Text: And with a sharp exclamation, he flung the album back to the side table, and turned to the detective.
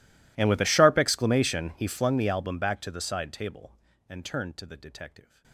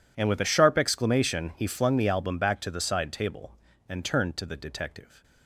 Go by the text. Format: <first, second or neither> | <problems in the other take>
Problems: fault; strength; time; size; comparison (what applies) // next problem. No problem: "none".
second | gets quieter; strong; throughout; 32 dB